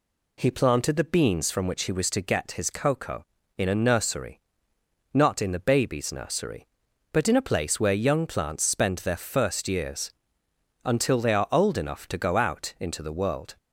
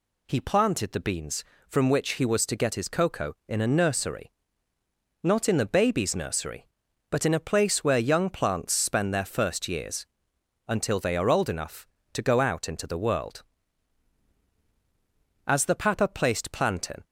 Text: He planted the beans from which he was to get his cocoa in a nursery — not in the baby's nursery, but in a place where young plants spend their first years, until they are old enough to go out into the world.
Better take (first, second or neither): first